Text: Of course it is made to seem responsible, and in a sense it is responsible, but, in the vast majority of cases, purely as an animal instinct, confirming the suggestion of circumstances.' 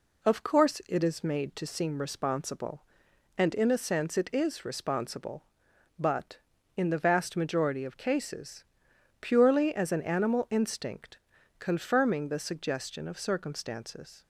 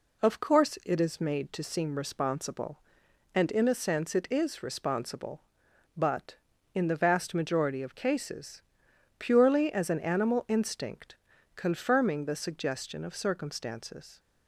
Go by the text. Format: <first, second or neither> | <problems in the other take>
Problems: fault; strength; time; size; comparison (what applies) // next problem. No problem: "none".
neither | none